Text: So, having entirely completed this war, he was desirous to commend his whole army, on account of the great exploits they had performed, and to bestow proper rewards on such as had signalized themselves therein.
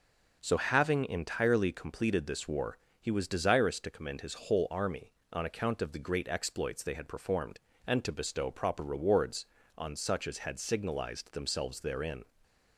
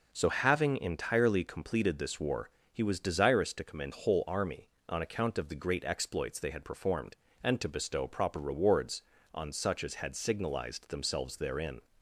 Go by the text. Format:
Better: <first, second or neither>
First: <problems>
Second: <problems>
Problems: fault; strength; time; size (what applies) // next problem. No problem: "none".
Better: first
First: none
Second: skips "his"; at 3.9 s